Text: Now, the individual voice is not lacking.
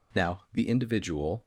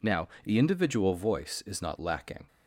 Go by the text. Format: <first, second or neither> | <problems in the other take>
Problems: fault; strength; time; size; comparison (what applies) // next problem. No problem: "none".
second | stops before "voice is not lacking"; at 1.4 s